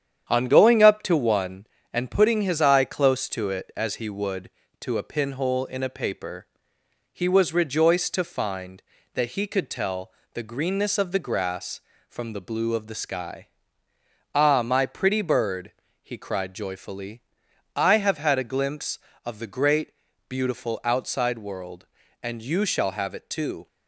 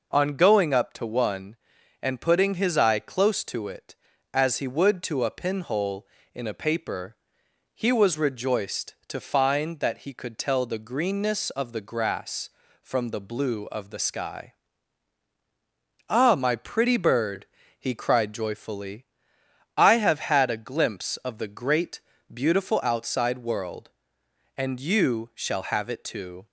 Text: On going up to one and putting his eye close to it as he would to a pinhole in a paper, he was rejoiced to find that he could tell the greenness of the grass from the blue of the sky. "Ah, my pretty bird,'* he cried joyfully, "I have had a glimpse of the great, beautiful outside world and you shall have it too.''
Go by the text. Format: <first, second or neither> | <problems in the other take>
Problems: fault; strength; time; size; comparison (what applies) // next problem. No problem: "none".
second | gets quieter; noticeable; throughout; 4.5 dB // pauses between "tell" and "the"; slight; at 10.1 s; 0.22 s long